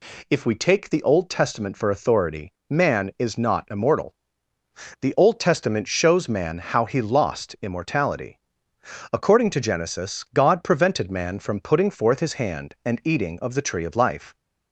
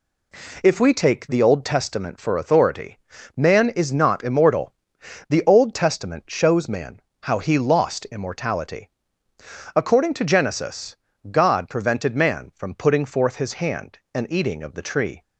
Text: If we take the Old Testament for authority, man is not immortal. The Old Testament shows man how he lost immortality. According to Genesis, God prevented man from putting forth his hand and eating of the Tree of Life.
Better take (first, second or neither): first